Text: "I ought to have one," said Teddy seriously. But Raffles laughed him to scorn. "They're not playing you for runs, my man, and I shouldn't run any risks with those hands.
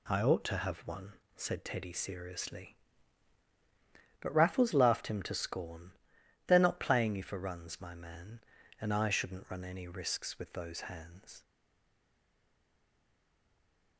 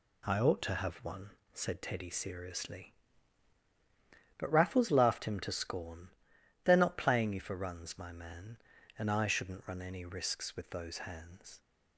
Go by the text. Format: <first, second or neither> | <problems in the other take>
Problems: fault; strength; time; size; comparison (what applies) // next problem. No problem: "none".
second | stays silent after the last word; strong; from 11.4 s on; 2.5 s long